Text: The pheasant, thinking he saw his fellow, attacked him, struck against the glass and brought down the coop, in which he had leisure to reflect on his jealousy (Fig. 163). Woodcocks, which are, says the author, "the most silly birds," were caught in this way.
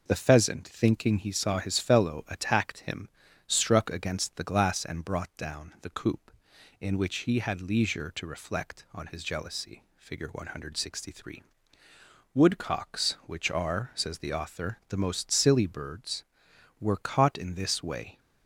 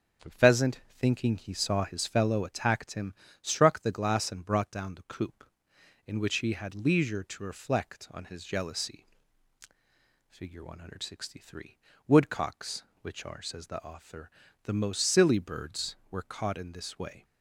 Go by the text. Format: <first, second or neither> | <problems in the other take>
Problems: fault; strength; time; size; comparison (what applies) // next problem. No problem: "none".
first | skips "against"; at 3.8 s